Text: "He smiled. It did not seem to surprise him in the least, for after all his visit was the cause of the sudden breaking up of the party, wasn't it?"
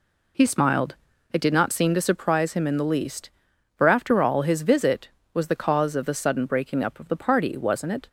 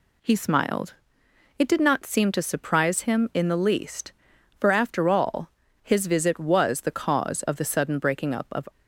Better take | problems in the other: first | pauses between "all" and "his"; slight; at 5.5 s; 0.32 s long // stops before "the party wasn't it"; at 8.6 s

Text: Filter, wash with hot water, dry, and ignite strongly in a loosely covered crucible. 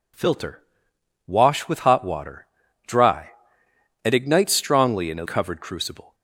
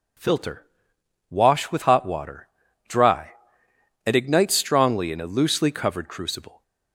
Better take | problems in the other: second | skips "loosely"; at 5.2 s

